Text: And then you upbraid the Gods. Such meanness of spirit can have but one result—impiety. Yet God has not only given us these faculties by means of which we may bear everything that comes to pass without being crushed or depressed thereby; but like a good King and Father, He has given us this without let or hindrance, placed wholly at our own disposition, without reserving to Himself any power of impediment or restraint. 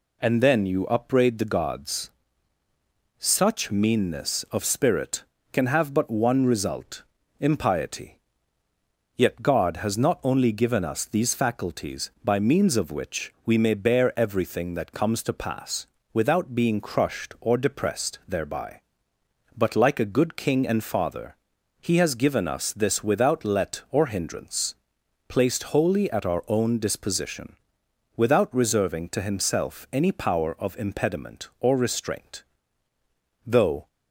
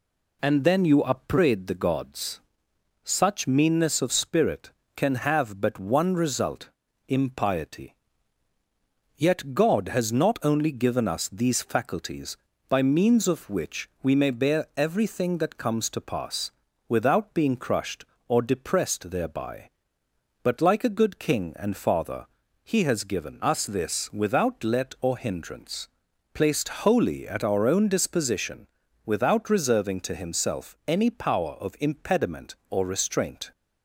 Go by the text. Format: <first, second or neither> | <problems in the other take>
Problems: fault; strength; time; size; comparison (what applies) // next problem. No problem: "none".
second | pauses between "pass" and "without"; slight; at 15.8 s; 0.26 s long; slight in the second // goes on to say "Though"; slight; from 33.4 s on; 0.40 s long